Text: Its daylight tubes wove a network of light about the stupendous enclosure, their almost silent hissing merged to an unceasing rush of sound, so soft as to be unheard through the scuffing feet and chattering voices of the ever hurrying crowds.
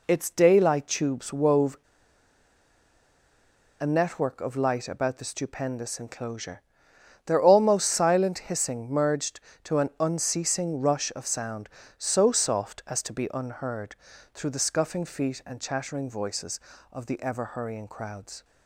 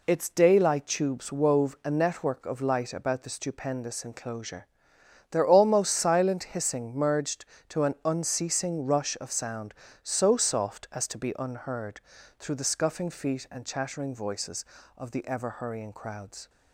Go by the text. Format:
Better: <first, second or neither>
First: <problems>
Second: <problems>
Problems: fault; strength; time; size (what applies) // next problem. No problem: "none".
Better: second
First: pauses between "wove" and "a"; strong; at 1.7 s; 2.0 s long // pauses between "unheard" and "through"; slight; at 13.9 s; 0.36 s long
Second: pauses between "unheard" and "through"; slight; at 12.0 s; 0.36 s long